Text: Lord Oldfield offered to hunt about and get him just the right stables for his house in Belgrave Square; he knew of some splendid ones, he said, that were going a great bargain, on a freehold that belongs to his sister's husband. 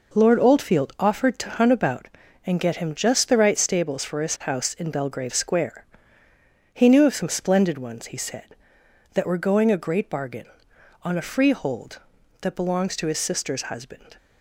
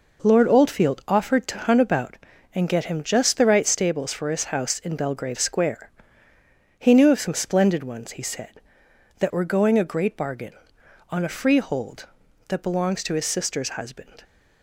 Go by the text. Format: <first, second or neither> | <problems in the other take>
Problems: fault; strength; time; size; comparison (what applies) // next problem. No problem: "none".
neither | none